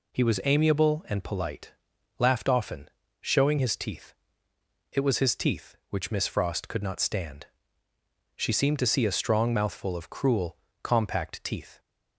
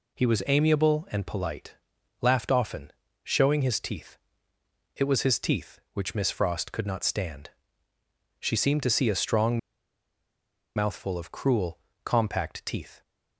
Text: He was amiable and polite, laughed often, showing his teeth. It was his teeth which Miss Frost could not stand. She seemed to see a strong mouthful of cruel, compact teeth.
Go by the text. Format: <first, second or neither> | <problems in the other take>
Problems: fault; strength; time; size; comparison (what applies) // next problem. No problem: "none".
first | pauses between "strong" and "mouthful"; at 9.5 s; 1.1 s long